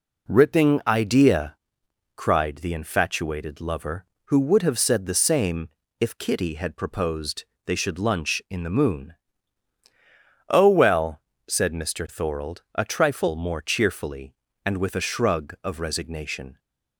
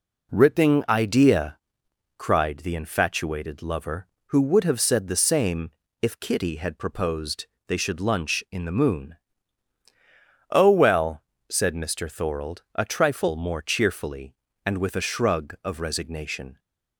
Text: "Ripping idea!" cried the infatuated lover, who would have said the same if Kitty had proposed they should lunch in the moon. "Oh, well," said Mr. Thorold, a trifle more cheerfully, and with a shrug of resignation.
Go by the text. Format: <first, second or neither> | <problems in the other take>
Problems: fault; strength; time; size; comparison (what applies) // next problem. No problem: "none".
neither | pauses between "same" and "if"; slight; the same in both // pauses between "proposed" and "they"; slight; the same in both